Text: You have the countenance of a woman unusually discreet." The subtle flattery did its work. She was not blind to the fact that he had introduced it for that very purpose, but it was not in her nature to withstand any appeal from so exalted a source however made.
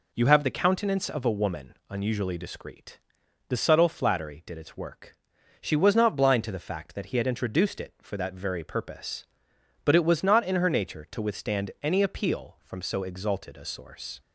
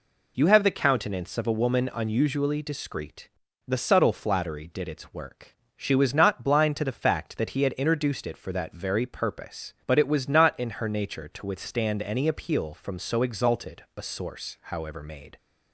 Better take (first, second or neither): second